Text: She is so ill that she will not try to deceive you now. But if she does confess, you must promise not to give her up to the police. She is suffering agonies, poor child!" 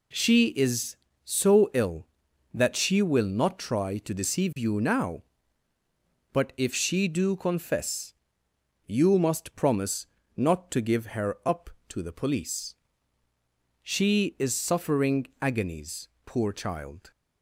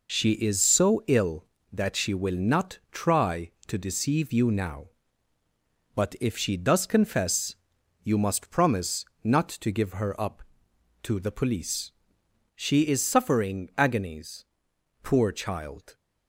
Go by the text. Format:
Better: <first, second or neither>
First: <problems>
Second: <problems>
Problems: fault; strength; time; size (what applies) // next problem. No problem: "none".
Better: second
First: says "do" for "does"; at 7.0 s // pauses between "promise" and "not"; slight; at 10.0 s; 0.30 s long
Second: pauses between "promise" and "not"; slight; at 9.0 s; 0.16 s long